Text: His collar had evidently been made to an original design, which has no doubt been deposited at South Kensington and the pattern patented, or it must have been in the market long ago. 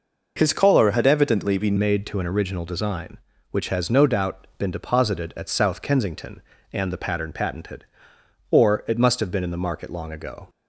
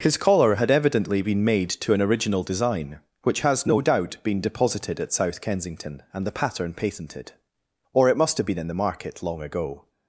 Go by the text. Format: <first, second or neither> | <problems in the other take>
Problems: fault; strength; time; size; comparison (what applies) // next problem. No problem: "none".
second | changes voice at "made"; from 1.7 s on; 8.7 s long